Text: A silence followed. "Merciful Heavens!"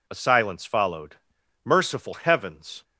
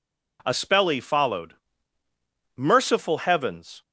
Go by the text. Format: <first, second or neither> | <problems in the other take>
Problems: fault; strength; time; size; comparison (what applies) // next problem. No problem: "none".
first | says "spelly" for "silence"; at 0.5 s